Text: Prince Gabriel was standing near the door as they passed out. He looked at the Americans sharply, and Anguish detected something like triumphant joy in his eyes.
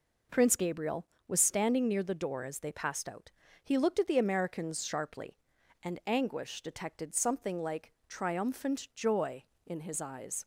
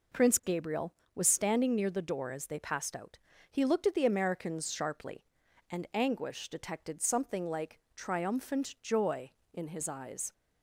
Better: neither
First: none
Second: none

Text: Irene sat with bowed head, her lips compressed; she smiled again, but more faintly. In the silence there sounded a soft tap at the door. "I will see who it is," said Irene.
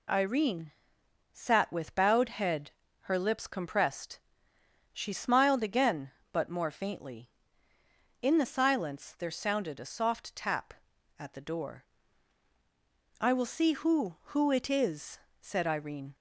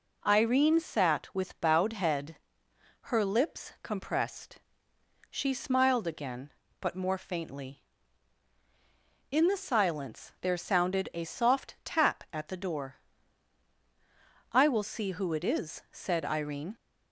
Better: second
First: pauses between "Irene" and "sat"; noticeable; at 0.7 s; 0.62 s long // says "who" twice; at 14.3 s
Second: none

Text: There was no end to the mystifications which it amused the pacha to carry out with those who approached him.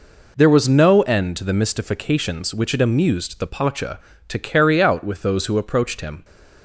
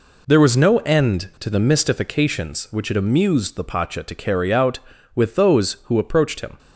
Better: neither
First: none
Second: none

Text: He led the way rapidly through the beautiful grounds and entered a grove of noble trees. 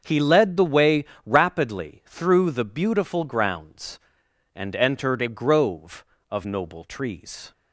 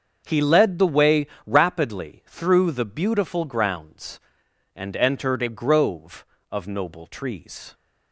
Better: neither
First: starts louder than the rest; until 1.0 s; 6.5 dB // pauses between "way" and "rapidly"; slight; at 1.0 s; 0.20 s long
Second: starts louder than the rest; until 1.2 s; 6.5 dB // pauses between "way" and "rapidly"; slight; at 1.2 s; 0.18 s long

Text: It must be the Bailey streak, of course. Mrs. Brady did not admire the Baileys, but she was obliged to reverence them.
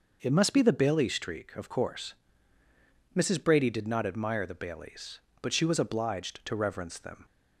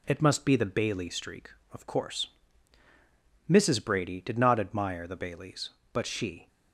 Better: first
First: none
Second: stops before "was obliged to reverence them"; at 6.4 s

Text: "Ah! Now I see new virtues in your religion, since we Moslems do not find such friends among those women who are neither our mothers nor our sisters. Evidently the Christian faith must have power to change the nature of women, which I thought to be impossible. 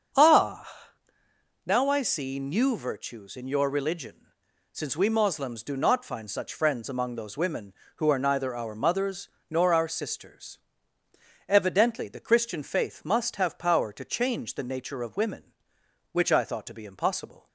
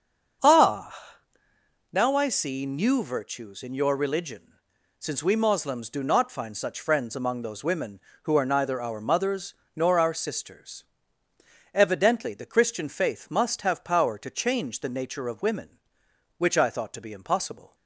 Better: neither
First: starts louder than the rest; until 2.0 s; 7 dB // pauses between "mothers" and "nor"; slight; at 9.2 s; 0.20 s long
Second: starts louder than the rest; until 2.3 s; 7 dB // pauses between "mothers" and "nor"; slight; at 9.5 s; 0.20 s long

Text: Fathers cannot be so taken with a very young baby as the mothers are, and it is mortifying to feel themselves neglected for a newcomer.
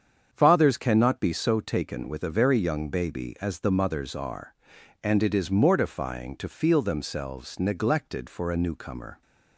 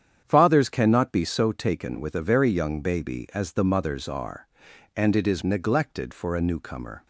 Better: first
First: starts louder than the rest; strong; until 1.3 s; 7.5 dB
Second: starts louder than the rest; strong; until 1.2 s; 8.5 dB // skips "mortifying to feel themselves"; at 5.4 s

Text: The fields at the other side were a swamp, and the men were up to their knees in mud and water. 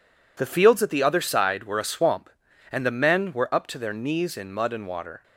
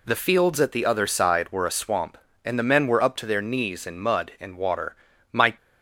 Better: first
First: none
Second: goes on to say "My"; slight; from 5.3 s on; 0.24 s long

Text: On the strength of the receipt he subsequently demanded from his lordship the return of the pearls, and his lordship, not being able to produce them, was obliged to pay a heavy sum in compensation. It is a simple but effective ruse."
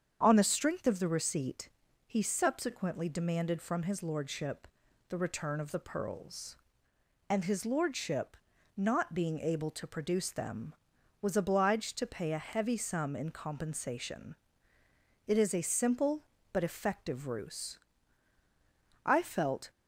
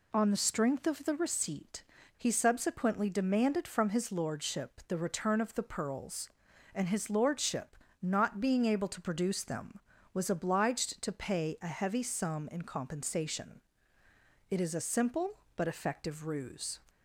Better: second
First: starts louder than the rest; strong; until 1.2 s; 7.5 dB // pauses between "receipt" and "he"; at 1.6 s; 0.38 s long // pauses between "lordship" and "the"; at 4.6 s; 0.42 s long // goes on to say "I felt"; noticeable; from 19.0 s on; 0.64 s long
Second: pauses between "receipt" and "he"; slight; at 1.8 s; 0.34 s long

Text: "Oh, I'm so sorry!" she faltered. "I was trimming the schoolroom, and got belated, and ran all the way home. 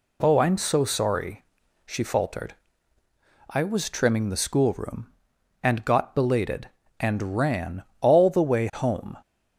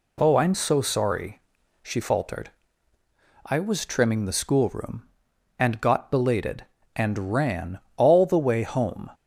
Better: neither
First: pauses between "ran" and "all"; slight; at 7.8 s; 0.18 s long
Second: pauses between "ran" and "all"; slight; at 7.7 s; 0.18 s long

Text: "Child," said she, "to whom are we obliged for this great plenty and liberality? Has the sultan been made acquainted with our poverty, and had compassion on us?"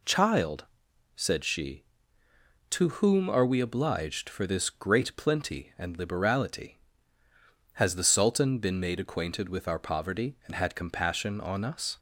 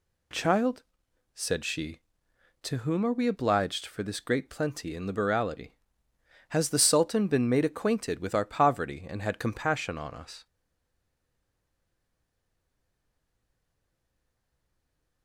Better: first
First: none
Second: stays silent after the last word; strong; from 10.4 s on; 4.8 s long

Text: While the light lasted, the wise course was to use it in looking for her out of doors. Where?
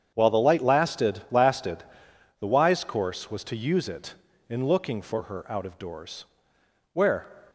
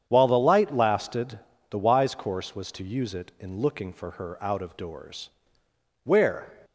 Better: second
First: starts louder than the rest; strong; until 1.1 s; 8 dB // says "lasted" twice; at 1.3 s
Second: starts louder than the rest; strong; until 1.1 s; 8.5 dB

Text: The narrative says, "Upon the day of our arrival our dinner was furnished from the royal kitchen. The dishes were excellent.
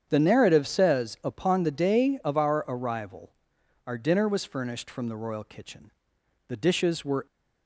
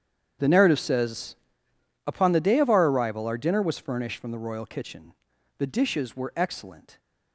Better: second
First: starts louder than the rest; strong; until 1.1 s; 8 dB // pauses between "arrival" and "our"; noticeable; at 3.3 s; 0.56 s long // stops before "excellent"; at 7.2 s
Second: starts louder than the rest; strong; until 2.1 s; 8.5 dB

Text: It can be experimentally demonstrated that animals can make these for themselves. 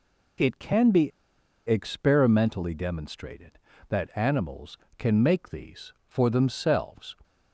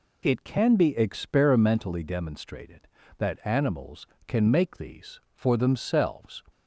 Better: second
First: pauses between "be" and "experimentally"; noticeable; at 1.1 s; 0.56 s long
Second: none

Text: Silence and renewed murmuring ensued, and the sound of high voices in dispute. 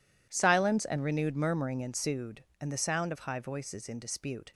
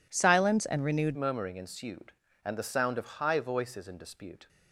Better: first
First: none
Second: changes voice at "murmuring"; from 1.1 s on; 3.3 s long

